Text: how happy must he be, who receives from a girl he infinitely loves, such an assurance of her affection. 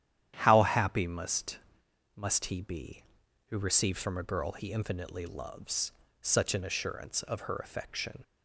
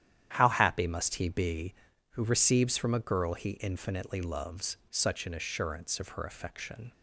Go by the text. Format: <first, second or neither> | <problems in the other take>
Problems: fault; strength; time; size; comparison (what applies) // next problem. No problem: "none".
second | starts louder than the rest; strong; until 1.3 s; 11 dB; strong in the second // says "must" twice; at 2.1 s